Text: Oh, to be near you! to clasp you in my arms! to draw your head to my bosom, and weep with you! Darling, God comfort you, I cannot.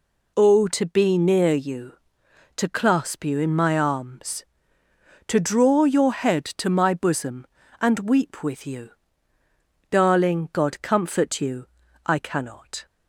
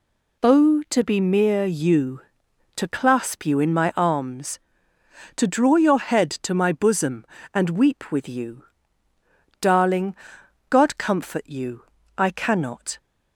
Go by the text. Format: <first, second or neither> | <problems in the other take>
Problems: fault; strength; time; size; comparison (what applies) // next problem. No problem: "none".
first | says "mere" for "near"; at 1.2 s